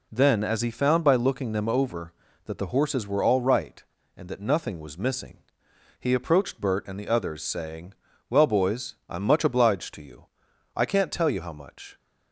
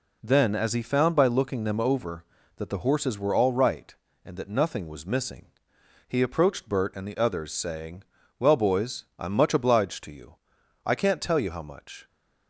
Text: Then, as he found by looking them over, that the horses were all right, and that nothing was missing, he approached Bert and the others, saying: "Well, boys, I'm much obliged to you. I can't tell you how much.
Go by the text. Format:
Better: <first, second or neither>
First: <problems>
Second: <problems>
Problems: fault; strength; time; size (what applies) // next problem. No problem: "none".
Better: neither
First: none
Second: none